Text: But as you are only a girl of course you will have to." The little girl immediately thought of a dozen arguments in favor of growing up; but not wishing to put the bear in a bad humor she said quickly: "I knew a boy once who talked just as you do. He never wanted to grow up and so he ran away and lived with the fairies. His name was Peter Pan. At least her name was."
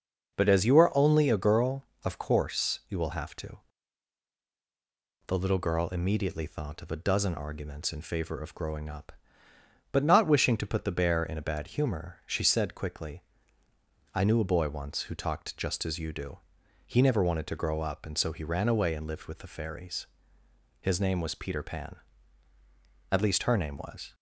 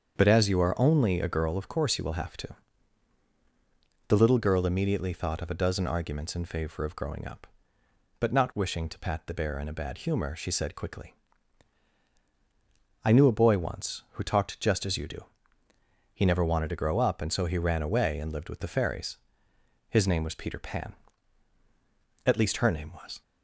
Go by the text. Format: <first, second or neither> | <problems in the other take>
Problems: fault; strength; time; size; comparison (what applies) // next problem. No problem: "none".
first | starts louder than the rest; strong; until 1.1 s; 7 dB // says "pat" for "put"; at 8.9 s